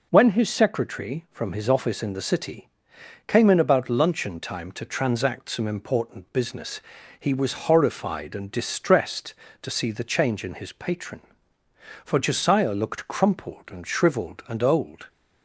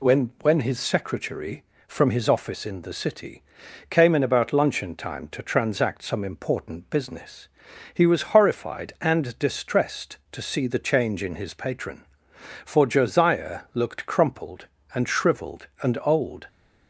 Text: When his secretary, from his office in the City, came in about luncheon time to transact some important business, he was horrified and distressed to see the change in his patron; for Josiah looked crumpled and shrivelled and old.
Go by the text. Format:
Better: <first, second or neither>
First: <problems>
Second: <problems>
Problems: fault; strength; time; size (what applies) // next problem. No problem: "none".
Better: first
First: none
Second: says "When" twice; at 0.4 s